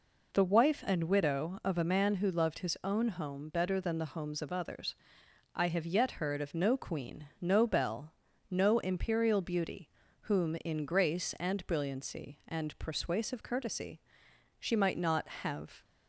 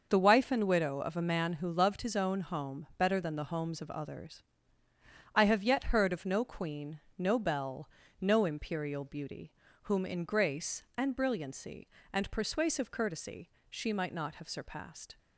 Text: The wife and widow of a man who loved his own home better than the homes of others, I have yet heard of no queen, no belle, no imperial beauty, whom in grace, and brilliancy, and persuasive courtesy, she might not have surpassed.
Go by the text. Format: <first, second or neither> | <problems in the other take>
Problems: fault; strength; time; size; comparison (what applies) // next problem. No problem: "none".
second | stops before "surpassed"; at 15.8 s